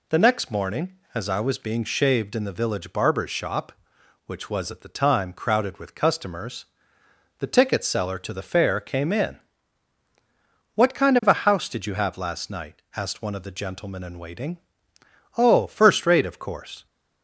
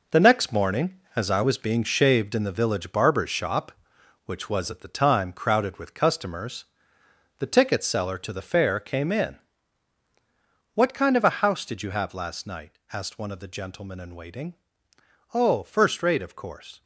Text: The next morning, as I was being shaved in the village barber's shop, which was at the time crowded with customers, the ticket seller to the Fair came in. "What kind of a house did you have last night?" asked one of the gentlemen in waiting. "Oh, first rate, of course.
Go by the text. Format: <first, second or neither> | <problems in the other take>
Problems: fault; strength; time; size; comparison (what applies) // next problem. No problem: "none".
first | gets quieter; strong; throughout; 9 dB